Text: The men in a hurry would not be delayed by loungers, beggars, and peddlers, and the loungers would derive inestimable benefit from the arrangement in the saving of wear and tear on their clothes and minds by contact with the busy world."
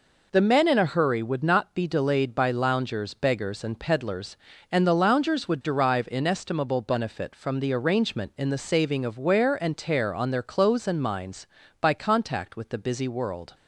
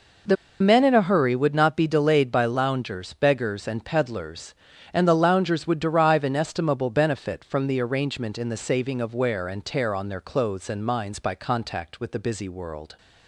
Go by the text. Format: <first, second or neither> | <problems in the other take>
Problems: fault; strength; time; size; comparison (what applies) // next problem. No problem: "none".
first | pauses between "The" and "men"; slight; at 0.3 s; 0.25 s long